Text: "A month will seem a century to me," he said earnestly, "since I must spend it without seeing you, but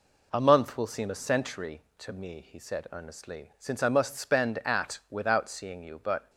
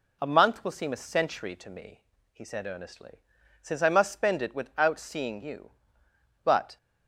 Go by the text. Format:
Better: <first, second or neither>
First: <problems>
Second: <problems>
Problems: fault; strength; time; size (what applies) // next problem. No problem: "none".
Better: second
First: says "at" for "it"; at 4.5 s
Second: none